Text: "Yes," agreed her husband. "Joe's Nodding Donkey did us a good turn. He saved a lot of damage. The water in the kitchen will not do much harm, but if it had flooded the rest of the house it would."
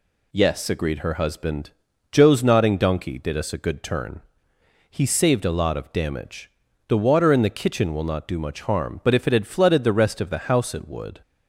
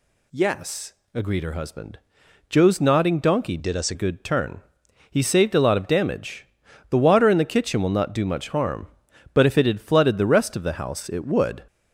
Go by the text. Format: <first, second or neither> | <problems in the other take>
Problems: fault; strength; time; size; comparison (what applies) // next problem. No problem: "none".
first | changes voice from "did" to "a"; from 3.5 to 3.9 s; 0.4 s long